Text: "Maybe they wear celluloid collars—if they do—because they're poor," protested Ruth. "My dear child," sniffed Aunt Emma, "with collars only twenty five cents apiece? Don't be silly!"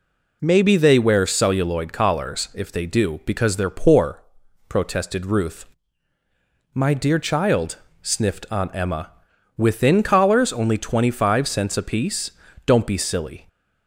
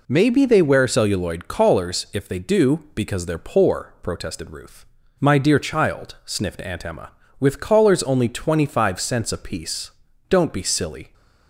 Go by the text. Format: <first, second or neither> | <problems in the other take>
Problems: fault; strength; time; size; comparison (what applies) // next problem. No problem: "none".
second | says "within" for "with"; at 9.5 s